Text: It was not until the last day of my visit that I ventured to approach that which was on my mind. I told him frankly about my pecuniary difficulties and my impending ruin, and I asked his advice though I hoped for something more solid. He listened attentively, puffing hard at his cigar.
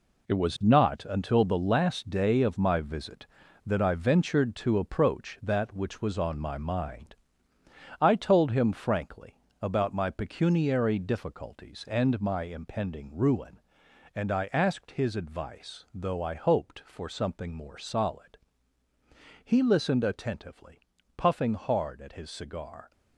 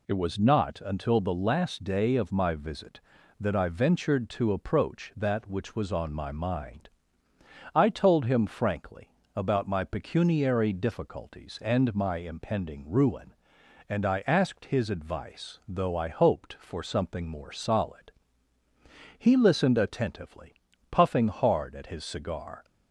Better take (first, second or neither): second